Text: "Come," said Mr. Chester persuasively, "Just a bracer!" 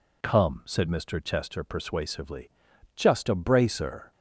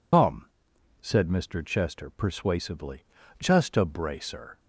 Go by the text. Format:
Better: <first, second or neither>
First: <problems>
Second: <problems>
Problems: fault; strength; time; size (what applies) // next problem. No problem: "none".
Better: first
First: none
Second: loses the start of "Come"; at 0.1 s; 105 ms